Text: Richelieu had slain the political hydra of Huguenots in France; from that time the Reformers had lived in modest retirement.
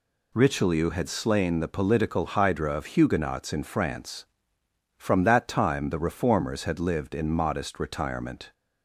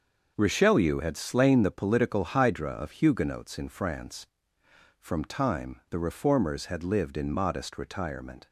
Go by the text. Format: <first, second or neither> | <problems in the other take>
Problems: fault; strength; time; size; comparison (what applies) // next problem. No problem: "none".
first | starts louder than the rest; until 1.3 s; 6.5 dB // skips "that"; at 5.2 s